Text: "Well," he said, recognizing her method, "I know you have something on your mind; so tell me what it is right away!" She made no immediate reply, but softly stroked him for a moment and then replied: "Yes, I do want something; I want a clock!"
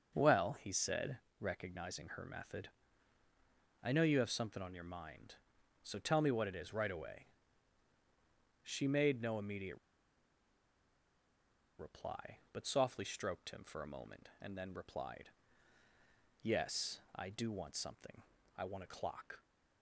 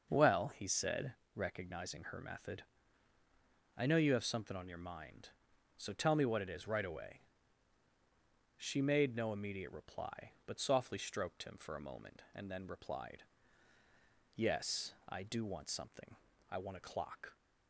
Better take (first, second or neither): second